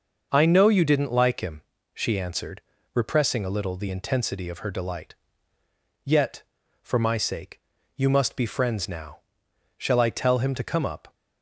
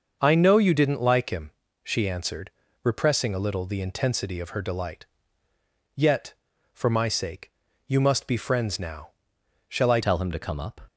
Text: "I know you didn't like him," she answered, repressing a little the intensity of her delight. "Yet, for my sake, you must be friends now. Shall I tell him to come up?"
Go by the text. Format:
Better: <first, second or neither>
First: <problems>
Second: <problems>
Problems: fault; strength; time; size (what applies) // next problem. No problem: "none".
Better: first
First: starts louder than the rest; noticeable; until 1.3 s; 6 dB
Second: starts louder than the rest; until 1.2 s; 6.5 dB // changes voice at "tell"; from 10.0 s on; 0.8 s long